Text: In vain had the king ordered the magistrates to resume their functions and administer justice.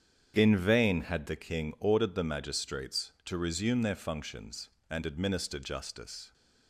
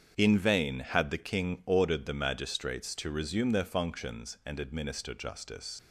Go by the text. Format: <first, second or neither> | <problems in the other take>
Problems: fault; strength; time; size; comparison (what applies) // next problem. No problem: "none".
first | starts louder than the rest; strong; until 1.1 s; 8 dB; strong in the first // leaves "justice" unfinished; at 5.7 s; 95 ms